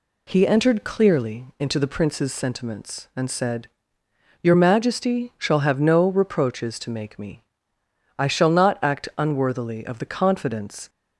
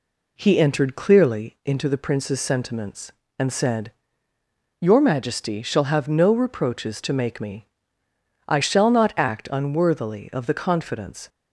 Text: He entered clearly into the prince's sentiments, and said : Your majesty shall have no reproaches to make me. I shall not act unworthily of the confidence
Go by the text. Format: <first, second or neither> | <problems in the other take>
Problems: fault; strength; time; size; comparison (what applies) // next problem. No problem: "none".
neither | none